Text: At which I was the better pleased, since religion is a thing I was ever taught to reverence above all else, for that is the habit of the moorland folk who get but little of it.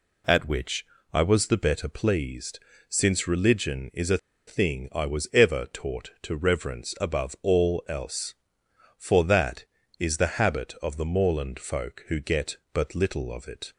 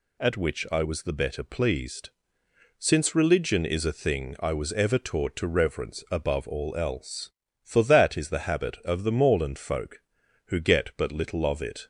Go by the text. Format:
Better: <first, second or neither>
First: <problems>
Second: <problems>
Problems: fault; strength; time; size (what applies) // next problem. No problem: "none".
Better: second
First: pauses between "which" and "I"; slight; at 0.8 s; 0.28 s long // pauses between "a" and "thing"; slight; at 4.1 s; 0.30 s long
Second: none